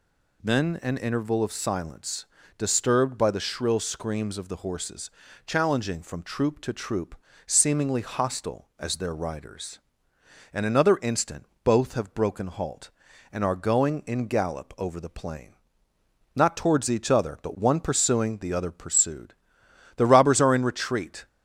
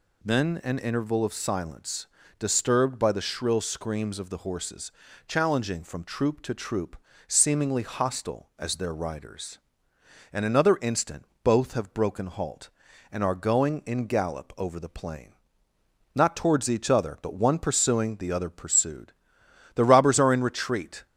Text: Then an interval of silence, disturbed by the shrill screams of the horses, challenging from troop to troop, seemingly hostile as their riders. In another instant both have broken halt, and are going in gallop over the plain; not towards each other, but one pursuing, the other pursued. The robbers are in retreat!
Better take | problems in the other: neither | pauses between "instant" and "both"; slight; the same in both

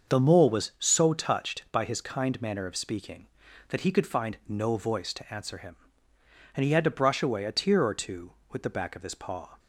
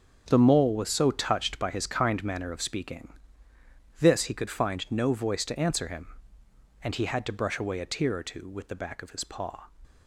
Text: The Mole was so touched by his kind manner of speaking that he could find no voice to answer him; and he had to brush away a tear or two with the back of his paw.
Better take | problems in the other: first | starts louder than the rest; strong; until 1.2 s; 7 dB; also in the first // says "this" for "that"; at 3.9 s

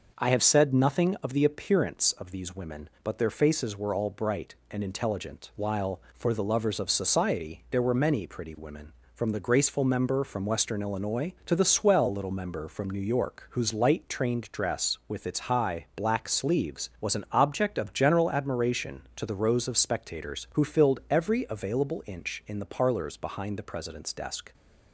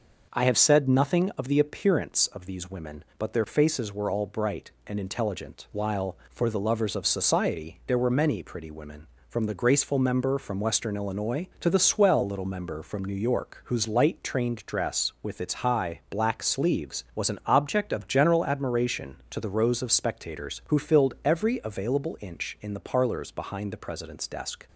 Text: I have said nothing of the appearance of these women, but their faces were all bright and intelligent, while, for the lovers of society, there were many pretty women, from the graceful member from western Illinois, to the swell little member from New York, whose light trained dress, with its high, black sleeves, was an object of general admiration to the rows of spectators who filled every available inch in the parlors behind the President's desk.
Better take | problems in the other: neither | none

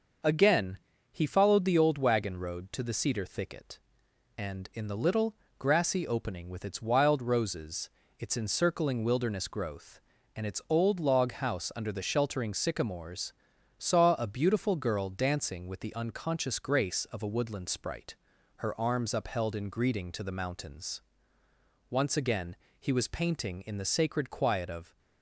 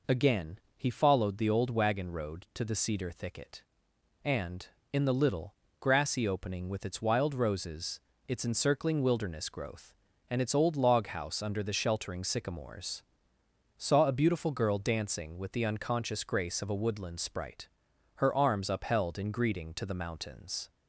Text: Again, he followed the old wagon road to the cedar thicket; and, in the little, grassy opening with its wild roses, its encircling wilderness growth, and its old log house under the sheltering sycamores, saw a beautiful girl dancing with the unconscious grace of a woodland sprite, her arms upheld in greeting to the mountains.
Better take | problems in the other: second | starts louder than the rest; noticeable; until 1.5 s; 6 dB // goes on to say "Once again he was painting in the sacred quiet of"; strong; from 21.8 s on; 3.0 s long

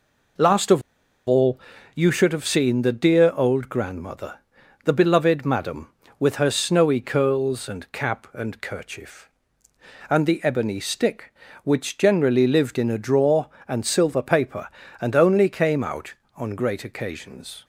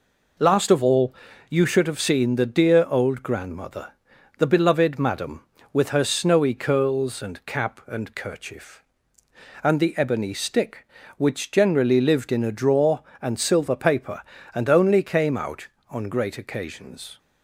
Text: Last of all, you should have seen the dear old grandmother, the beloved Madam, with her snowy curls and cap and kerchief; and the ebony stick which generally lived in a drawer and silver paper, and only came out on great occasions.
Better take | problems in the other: second | pauses between "of" and "all"; noticeable; at 0.8 s; 0.46 s long

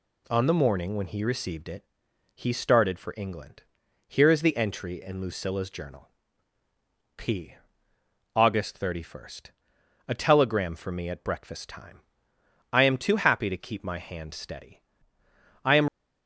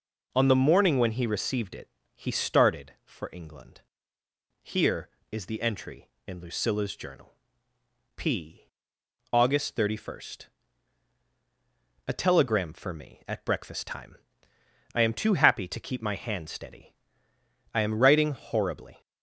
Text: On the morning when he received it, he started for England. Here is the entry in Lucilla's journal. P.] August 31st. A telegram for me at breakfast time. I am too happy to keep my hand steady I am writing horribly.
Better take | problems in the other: second | pauses between "steady" and "I"; noticeable; at 14.8 s; 0.84 s long; noticeable in the second // stops before "writing horribly"; at 15.8 s

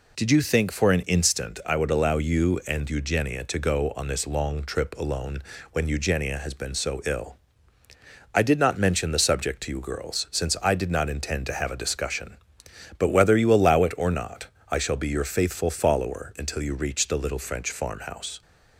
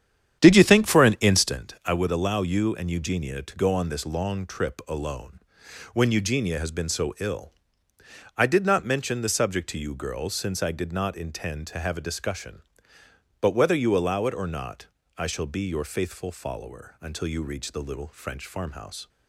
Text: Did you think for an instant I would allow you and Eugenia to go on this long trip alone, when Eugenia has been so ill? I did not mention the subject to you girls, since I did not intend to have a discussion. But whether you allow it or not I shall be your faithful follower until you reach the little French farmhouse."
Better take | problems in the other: first | starts louder than the rest; strong; until 1.7 s; 9.5 dB // pauses between "not" and "I"; slight; at 14.8 s; 0.30 s long; slight in the first

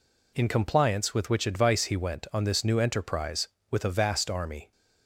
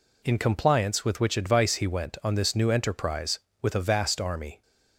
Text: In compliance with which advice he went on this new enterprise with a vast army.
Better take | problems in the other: neither | none

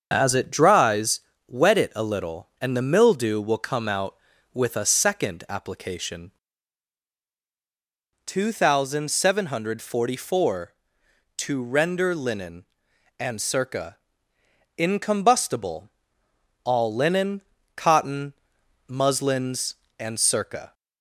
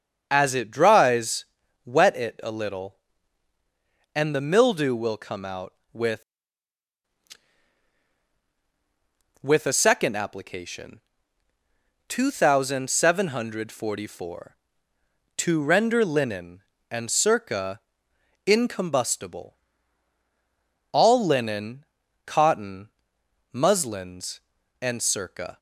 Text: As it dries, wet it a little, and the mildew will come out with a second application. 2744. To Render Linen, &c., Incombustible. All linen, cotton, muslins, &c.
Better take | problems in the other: first | starts louder than the rest; until 1.3 s; 7 dB; also in the first // says "with" twice; at 9.4 s

